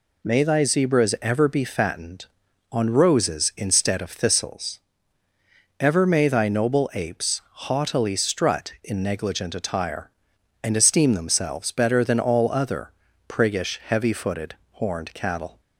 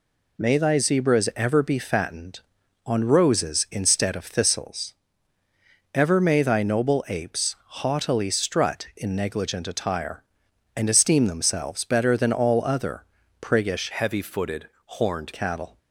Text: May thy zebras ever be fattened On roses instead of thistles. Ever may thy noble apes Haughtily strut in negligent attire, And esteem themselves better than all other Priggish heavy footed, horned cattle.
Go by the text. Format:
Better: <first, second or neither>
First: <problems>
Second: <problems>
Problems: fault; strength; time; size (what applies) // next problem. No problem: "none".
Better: first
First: pauses between "apes" and "Haughtily"; slight; at 7.4 s; 0.26 s long // pauses between "other" and "Priggish"; slight; at 12.9 s; 0.36 s long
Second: pauses between "apes" and "Haughtily"; slight; at 7.5 s; 0.26 s long // pauses between "other" and "Priggish"; slight; at 13.0 s; 0.36 s long // changes voice from "heavy" to "horned"; from 13.9 to 15.3 s; 1.4 s long